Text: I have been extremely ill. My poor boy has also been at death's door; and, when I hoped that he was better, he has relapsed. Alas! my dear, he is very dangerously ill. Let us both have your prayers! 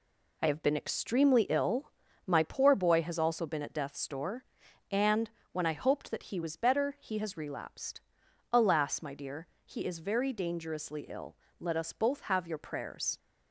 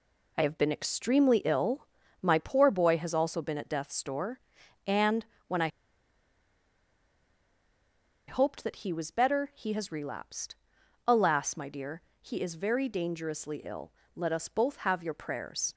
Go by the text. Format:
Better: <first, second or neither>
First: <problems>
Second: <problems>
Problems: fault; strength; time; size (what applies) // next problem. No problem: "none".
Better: first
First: none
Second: pauses between "I" and "hoped"; strong; at 5.6 s; 2.5 s long